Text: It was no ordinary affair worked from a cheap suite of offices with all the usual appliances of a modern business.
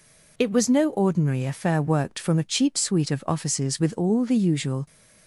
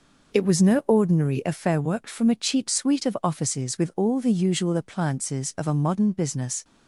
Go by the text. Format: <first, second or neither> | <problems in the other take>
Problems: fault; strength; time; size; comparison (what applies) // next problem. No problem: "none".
second | stops before "appliances of a modern business"; at 4.8 s